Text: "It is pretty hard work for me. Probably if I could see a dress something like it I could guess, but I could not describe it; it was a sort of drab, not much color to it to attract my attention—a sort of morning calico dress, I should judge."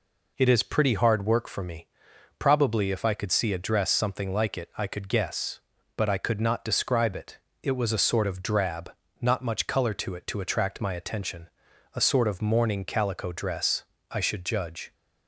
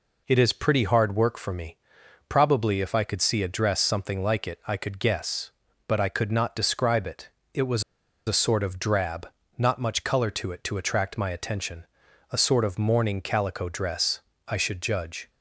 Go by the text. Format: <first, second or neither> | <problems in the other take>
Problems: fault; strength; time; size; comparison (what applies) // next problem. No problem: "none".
first | pauses between "was" and "a"; at 7.8 s; 0.44 s long